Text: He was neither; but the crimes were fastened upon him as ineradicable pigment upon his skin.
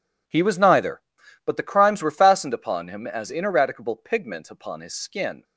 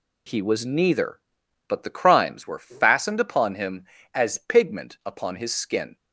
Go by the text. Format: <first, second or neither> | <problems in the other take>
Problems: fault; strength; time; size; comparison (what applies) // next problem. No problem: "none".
first | skips "ineradicable"; at 4.3 s